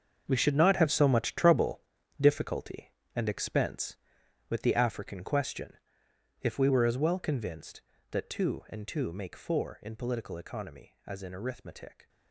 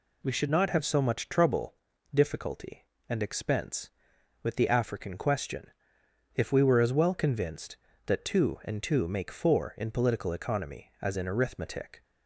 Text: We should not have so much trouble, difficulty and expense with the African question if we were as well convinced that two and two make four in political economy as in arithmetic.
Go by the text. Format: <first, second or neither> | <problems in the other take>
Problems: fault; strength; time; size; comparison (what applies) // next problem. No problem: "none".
second | gets quieter; strong; throughout; 13.5 dB // pauses between "question" and "if"; noticeable; at 5.7 s; 0.68 s long; noticeable in the second